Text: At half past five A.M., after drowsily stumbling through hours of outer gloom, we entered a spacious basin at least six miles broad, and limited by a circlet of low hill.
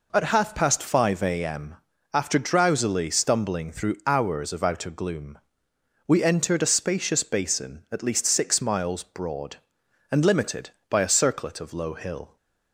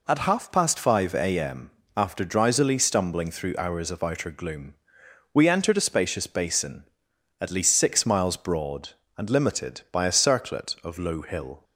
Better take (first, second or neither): neither